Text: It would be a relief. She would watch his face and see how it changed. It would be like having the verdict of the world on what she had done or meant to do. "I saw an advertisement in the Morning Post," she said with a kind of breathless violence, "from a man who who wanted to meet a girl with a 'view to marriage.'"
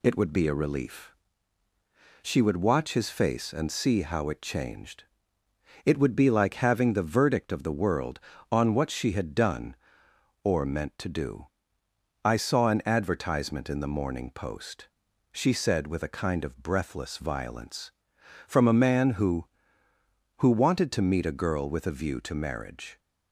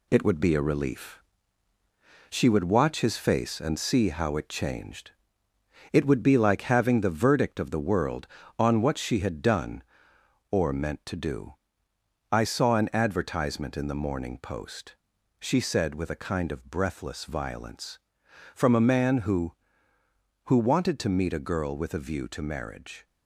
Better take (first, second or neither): first